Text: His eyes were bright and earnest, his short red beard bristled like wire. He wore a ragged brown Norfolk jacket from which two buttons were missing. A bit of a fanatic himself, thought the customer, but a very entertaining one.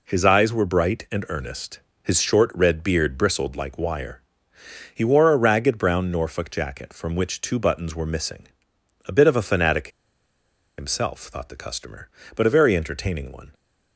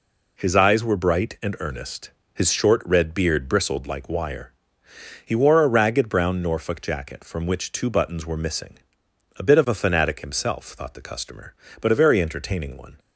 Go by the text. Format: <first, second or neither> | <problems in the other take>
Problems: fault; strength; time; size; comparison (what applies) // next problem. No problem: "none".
second | pauses between "fanatic" and "himself"; noticeable; at 9.8 s; 0.89 s long